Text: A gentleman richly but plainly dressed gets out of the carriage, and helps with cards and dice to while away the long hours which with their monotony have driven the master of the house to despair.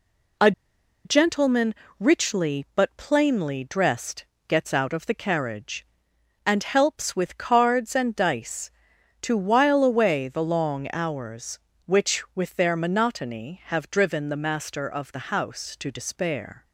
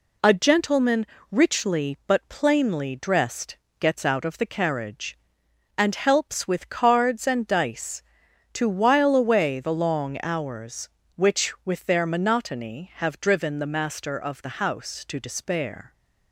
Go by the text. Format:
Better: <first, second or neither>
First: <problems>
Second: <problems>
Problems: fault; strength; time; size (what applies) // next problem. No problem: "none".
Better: second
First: pauses between "A" and "gentleman"; noticeable; at 0.5 s; 0.53 s long // pauses between "gentleman" and "richly"; slight; at 1.7 s; 0.26 s long // pauses between "dressed" and "gets"; slight; at 4.2 s; 0.24 s long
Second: pauses between "gentleman" and "richly"; slight; at 1.0 s; 0.26 s long // pauses between "dressed" and "gets"; slight; at 3.5 s; 0.24 s long